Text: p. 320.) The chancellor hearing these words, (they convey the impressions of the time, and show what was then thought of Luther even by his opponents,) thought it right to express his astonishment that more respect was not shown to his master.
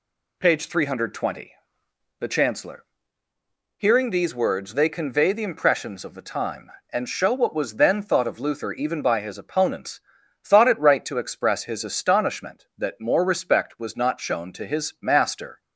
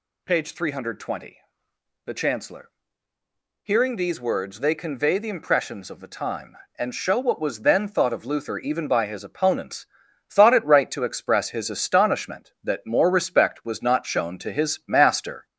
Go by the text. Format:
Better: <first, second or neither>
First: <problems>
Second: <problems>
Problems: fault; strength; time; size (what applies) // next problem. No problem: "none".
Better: first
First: pauses between "chancellor" and "hearing"; noticeable; at 2.8 s; 0.92 s long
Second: gets louder; slight; throughout; 2.5 dB // pauses between "chancellor" and "hearing"; noticeable; at 2.6 s; 0.92 s long